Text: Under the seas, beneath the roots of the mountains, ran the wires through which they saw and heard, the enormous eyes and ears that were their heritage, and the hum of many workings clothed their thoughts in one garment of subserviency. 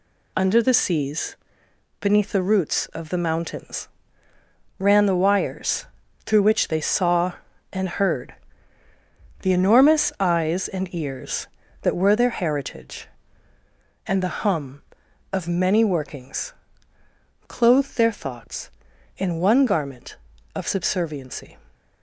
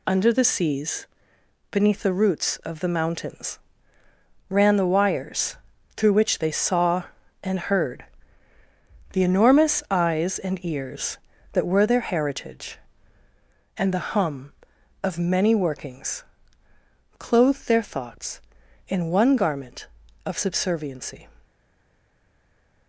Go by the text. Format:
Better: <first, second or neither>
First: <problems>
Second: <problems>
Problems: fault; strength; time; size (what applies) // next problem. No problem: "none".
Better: first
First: pauses between "wires" and "through"; at 5.8 s; 0.38 s long // pauses between "workings" and "clothed"; noticeable; at 16.5 s; 0.96 s long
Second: pauses between "wires" and "through"; at 5.5 s; 0.38 s long // pauses between "workings" and "clothed"; noticeable; at 16.2 s; 0.96 s long // stays silent after the last word; noticeable; from 21.4 s on; 1.4 s long